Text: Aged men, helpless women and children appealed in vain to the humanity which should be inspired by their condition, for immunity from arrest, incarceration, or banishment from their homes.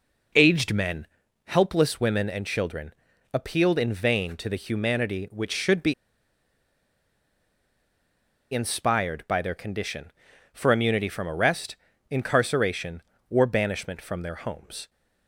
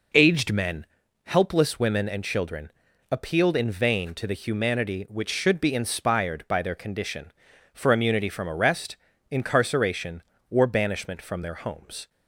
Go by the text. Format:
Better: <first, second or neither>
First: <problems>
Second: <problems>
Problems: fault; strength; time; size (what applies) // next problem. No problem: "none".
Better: second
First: pauses between "children" and "appealed"; at 2.9 s; 0.42 s long // pauses between "be" and "inspired"; strong; at 5.9 s; 2.5 s long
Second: pauses between "children" and "appealed"; at 2.7 s; 0.42 s long